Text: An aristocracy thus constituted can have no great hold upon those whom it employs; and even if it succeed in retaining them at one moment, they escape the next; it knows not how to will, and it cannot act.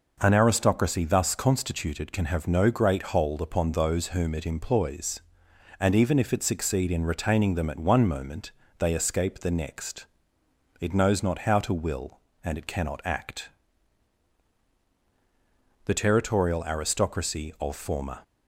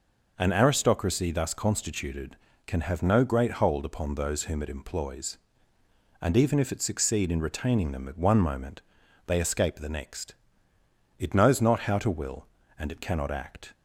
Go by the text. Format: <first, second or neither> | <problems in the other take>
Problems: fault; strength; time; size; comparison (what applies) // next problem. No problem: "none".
second | goes on to say "The territorial aristocracy of former"; strong; from 15.8 s on; 2.3 s long